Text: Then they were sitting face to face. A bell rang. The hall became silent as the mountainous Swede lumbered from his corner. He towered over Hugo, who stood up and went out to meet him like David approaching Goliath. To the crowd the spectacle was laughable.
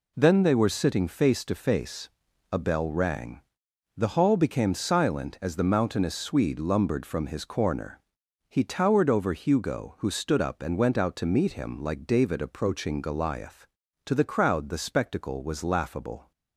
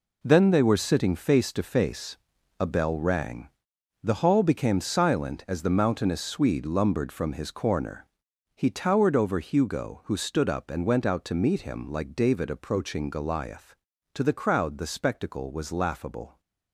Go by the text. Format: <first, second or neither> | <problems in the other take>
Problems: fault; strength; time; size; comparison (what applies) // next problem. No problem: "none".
first | gets quieter; strong; throughout; 10 dB